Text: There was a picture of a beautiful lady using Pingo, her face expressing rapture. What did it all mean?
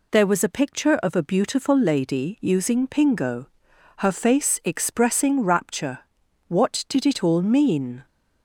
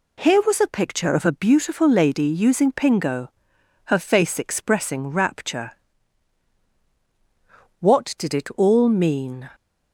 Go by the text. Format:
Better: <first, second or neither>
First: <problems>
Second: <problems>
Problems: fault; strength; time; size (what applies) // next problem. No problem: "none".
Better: first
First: none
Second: says "Here" for "There"; at 0.2 s